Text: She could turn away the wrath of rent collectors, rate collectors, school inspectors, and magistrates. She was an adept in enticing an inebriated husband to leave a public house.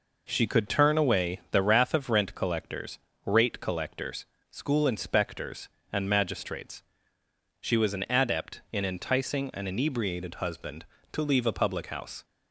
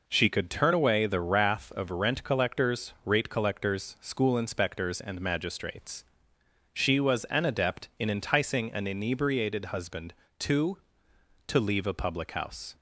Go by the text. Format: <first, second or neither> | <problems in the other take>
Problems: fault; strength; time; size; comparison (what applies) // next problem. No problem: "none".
first | says "to" twice; at 11.4 s